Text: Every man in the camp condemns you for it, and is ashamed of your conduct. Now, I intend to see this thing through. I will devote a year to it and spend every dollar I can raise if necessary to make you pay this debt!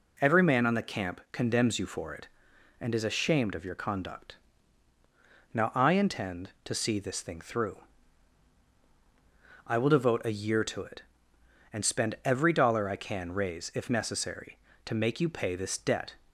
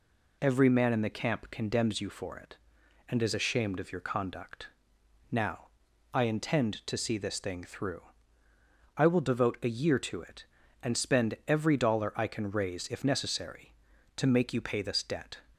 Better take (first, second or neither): second